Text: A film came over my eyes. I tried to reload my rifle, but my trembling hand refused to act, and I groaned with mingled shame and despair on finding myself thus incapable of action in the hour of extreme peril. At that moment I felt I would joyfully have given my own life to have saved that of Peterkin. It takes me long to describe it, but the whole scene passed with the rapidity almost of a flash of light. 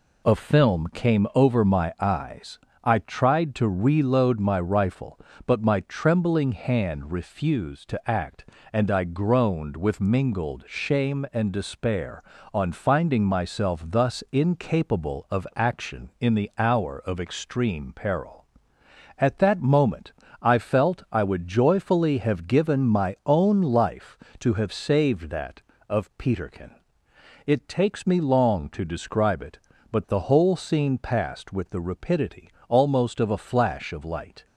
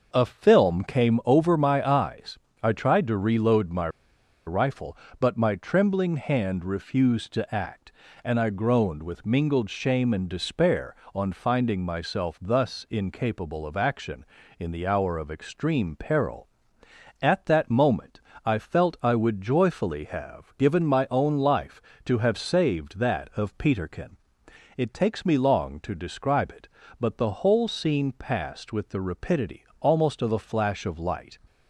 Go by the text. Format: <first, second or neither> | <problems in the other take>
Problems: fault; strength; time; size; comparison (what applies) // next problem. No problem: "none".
first | pauses between "my" and "rifle"; noticeable; at 3.8 s; 0.58 s long // pauses between "moment" and "I"; slight; at 18.1 s; 0.24 s long; slight in the first // pauses between "rapidity" and "almost"; slight; at 29.6 s; 0.16 s long; slight in the first